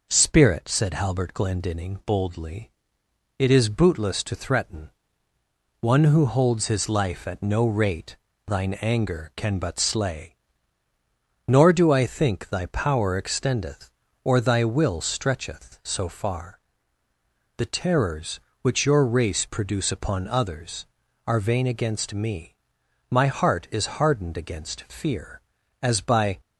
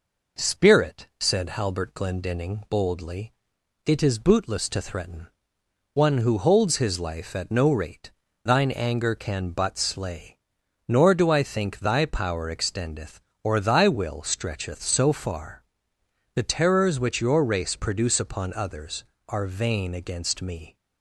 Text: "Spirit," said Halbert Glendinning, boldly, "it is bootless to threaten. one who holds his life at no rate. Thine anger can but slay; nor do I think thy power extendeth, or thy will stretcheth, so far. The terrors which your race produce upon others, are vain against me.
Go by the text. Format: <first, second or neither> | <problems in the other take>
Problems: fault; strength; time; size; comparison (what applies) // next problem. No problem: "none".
second | goes on to say "My heart is hardened against fear as by"; strong; from 23.0 s on; 3.3 s long